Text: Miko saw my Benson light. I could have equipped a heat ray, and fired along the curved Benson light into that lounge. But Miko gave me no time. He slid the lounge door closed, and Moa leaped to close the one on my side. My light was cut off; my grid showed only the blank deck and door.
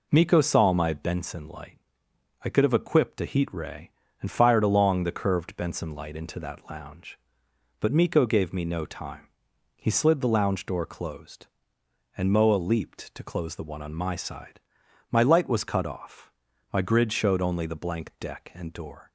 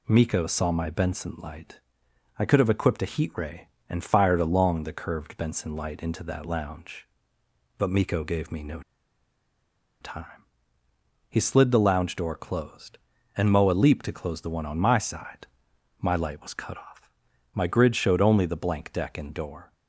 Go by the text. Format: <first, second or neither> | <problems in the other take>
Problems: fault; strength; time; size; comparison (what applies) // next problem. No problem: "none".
first | pauses between "no" and "time"; at 8.8 s; 1.2 s long